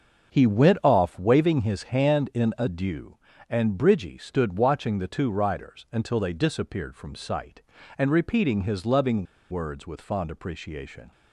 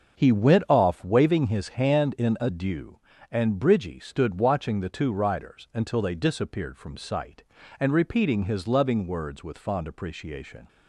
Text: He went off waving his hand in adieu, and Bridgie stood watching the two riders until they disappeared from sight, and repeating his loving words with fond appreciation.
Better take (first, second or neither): second